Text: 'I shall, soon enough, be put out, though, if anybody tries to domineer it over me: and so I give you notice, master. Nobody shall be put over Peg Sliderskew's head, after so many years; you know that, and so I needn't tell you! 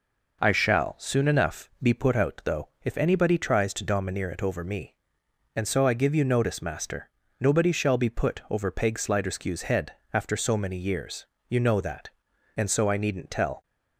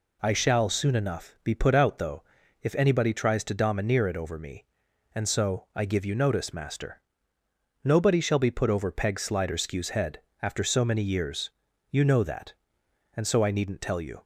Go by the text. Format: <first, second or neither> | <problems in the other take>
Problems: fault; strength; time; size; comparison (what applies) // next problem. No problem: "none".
second | stops before "you"; at 13.6 s